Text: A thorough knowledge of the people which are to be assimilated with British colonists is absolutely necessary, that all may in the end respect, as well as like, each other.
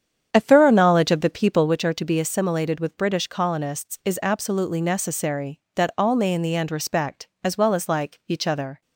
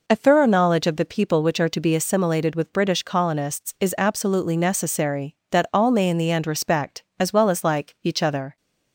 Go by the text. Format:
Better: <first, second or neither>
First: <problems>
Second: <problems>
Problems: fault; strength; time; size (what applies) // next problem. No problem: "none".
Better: second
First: starts louder than the rest; strong; until 1.8 s; 8.5 dB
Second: none